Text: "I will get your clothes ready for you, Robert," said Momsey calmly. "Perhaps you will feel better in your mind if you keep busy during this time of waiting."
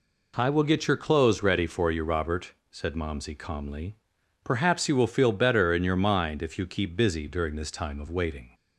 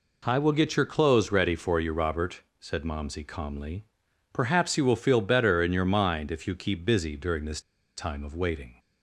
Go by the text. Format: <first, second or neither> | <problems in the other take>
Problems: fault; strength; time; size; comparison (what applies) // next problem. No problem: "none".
first | pauses between "this" and "time"; at 7.5 s; 0.37 s long